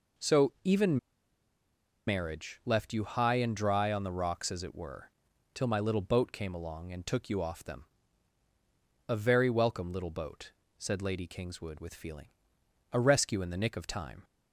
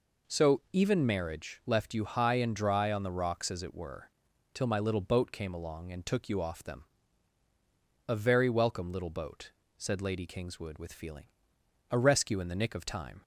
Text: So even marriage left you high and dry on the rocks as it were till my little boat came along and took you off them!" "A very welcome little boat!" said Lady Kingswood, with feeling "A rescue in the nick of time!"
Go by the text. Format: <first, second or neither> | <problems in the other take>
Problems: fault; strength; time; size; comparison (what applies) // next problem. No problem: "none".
second | pauses between "even" and "marriage"; at 0.9 s; 1.0 s long // pauses between "were" and "till"; at 5.0 s; 0.44 s long; also in the second // pauses between "feeling" and "A"; noticeable; at 12.2 s; 0.64 s long; noticeable in the second